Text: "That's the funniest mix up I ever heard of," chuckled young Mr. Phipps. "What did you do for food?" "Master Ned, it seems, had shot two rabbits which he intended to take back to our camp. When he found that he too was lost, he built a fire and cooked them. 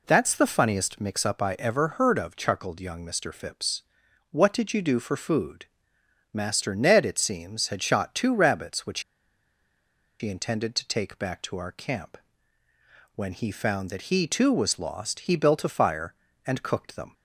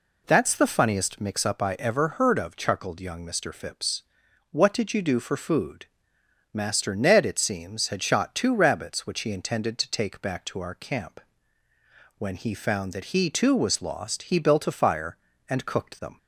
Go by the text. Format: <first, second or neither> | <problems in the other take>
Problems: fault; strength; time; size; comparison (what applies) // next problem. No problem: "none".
second | pauses between "which" and "he"; at 8.9 s; 1.2 s long